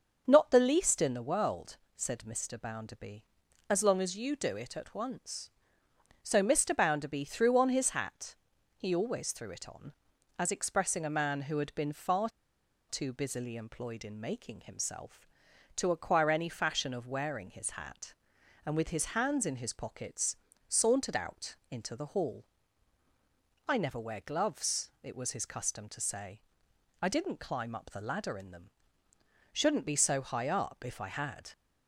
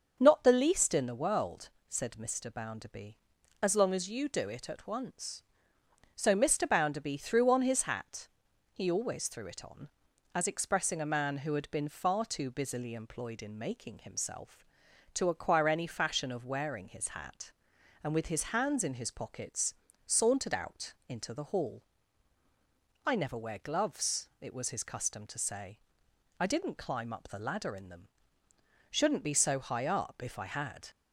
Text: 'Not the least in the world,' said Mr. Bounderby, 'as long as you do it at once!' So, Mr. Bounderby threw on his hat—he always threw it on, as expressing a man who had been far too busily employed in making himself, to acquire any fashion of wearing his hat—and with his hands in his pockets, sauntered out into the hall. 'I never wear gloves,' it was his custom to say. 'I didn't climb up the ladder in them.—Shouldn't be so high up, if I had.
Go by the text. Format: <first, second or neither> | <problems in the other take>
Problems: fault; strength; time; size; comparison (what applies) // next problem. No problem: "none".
second | starts louder than the rest; until 1.2 s; 6.5 dB; also in the second // pauses between "far" and "too"; noticeable; at 12.2 s; 0.61 s long